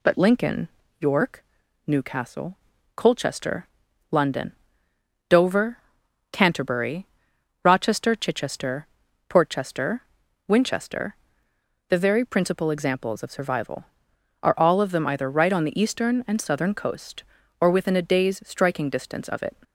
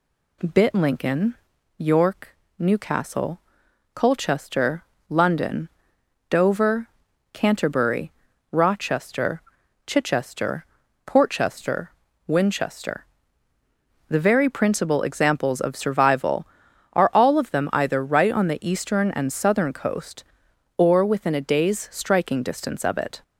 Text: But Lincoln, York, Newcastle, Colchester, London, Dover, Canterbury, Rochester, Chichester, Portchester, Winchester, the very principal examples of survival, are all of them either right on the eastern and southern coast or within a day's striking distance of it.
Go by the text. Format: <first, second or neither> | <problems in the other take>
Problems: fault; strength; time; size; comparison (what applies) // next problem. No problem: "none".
first | says "Bit" for "But"; at 0.5 s